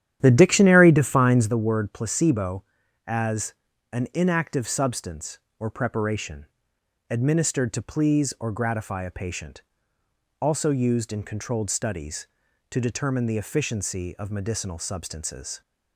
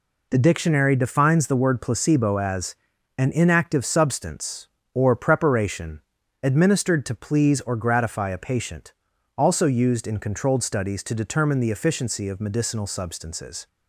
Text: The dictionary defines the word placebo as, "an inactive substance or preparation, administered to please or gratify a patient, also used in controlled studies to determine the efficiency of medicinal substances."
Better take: second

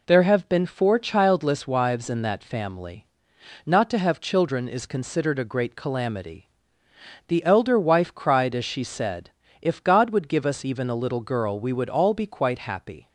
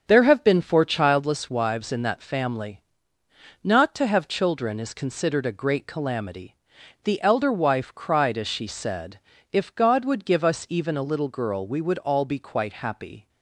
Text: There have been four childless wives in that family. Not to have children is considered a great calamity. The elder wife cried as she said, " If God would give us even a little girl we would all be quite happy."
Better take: first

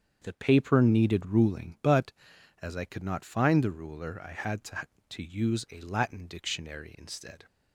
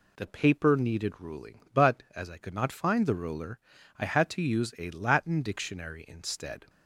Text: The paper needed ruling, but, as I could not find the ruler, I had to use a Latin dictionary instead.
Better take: second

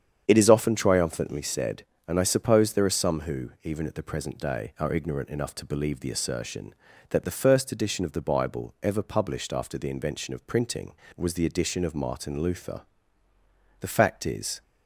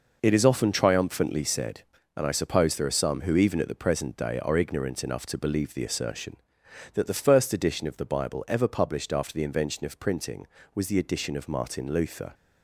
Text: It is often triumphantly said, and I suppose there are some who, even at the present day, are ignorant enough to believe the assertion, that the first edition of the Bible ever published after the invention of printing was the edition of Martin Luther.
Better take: second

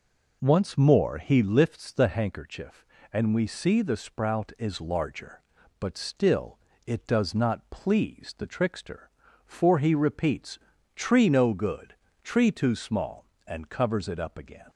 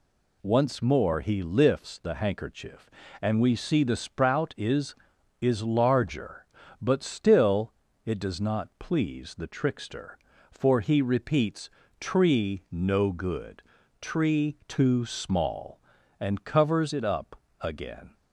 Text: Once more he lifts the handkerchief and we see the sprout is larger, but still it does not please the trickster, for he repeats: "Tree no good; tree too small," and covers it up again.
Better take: first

